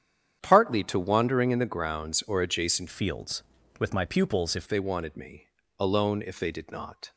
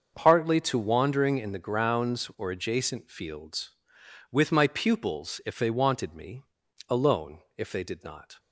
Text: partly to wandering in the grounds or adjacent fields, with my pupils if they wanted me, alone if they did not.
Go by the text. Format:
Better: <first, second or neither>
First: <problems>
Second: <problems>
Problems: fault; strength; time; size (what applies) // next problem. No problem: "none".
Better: second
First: starts louder than the rest; strong; until 1.4 s; 9 dB // changes voice from "fields" to "if"; from 2.8 to 4.6 s; 1.8 s long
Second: starts louder than the rest; until 1.1 s; 6.5 dB